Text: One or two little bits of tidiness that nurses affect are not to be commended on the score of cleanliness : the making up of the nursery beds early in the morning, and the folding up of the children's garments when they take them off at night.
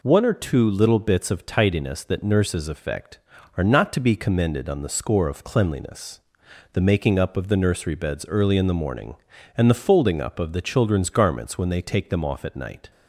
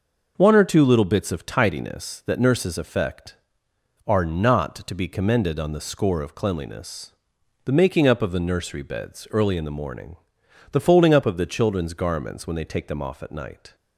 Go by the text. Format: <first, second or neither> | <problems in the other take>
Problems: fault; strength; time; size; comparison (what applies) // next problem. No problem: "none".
first | skips "and"; at 10.4 s